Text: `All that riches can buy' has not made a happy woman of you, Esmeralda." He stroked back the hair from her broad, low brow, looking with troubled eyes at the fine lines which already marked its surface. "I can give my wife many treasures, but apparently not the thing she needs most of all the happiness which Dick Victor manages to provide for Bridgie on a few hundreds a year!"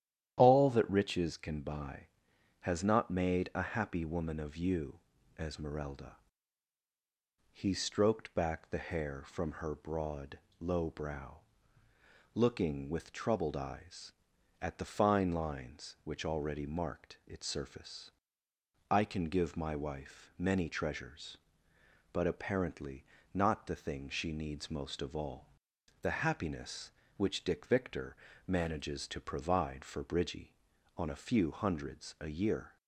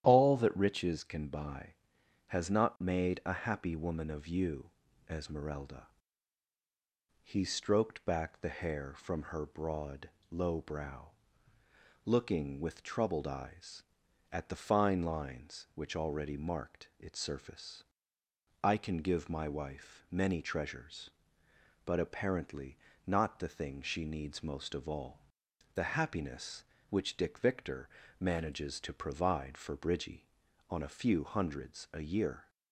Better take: neither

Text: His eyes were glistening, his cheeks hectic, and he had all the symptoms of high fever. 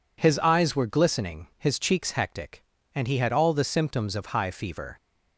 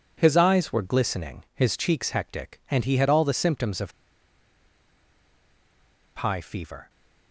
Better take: first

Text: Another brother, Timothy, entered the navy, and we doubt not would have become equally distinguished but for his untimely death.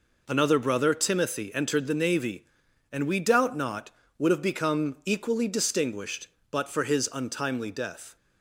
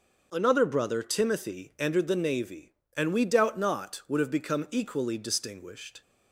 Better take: first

